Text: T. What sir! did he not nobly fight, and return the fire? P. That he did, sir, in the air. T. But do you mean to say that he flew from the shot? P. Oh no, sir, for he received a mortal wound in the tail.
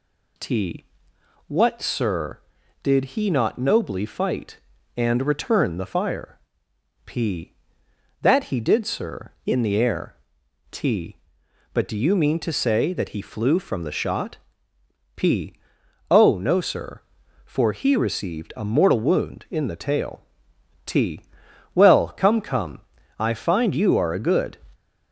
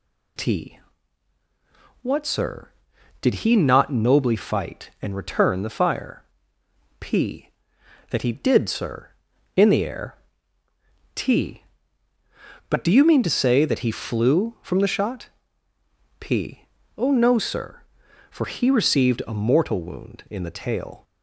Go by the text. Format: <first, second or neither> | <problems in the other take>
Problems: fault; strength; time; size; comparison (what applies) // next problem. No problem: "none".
second | goes on to say "T Well come come I find you are a good"; strong; from 20.8 s on; 3.7 s long